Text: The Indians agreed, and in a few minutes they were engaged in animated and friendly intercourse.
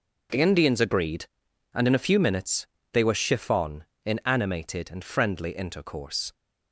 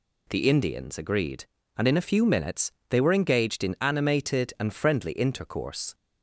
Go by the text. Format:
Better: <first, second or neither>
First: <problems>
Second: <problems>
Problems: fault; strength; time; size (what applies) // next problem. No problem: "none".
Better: second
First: pauses between "minutes" and "they"; slight; at 2.6 s; 0.28 s long // says "chiffon" for "engaged"; at 3.1 s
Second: pauses between "minutes" and "they"; slight; at 2.7 s; 0.18 s long